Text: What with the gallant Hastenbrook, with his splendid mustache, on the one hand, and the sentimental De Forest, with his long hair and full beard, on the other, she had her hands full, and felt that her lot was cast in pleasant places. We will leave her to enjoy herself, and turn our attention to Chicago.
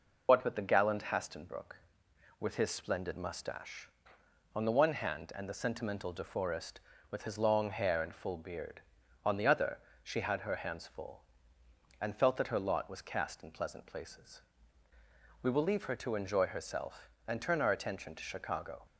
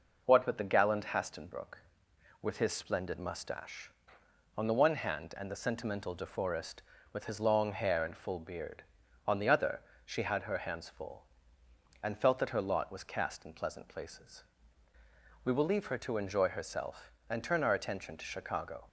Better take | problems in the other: second | loses the start of "What"; at 0.2 s; 60 ms

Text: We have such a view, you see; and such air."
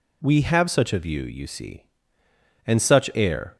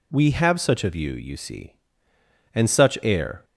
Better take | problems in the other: neither | none

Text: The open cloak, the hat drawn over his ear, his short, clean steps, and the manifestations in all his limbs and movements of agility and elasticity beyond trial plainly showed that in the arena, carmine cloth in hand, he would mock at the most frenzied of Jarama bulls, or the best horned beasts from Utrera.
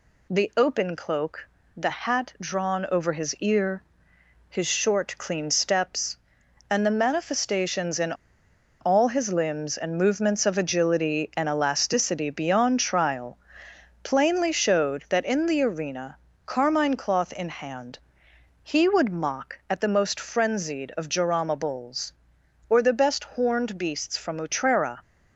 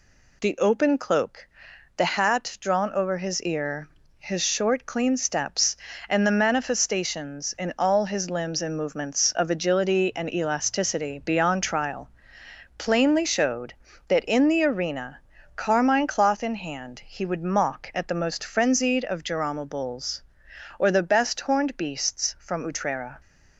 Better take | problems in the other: second | pauses between "in" and "all"; noticeable; at 8.1 s; 0.66 s long // pauses between "trial" and "plainly"; noticeable; at 13.3 s; 0.66 s long; noticeable in the second

